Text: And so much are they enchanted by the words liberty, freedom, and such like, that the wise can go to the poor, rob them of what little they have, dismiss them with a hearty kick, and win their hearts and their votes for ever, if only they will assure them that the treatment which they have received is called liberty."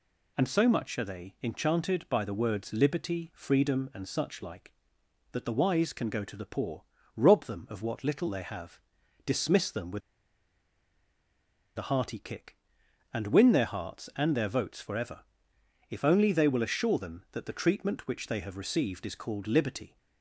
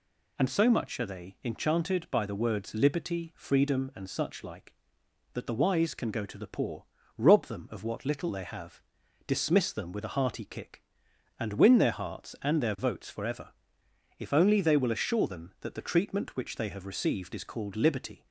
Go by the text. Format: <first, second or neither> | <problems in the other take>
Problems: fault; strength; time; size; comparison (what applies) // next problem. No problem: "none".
second | pauses between "with" and "a"; strong; at 10.0 s; 1.7 s long